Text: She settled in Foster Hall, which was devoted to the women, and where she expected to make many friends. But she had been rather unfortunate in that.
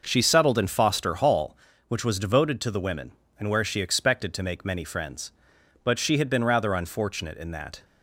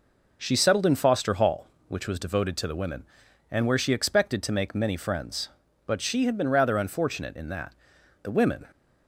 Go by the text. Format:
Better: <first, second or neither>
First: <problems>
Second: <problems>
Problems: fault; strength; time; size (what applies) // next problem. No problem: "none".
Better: first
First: none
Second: goes on to say "The women"; slight; from 8.2 s on; 0.42 s long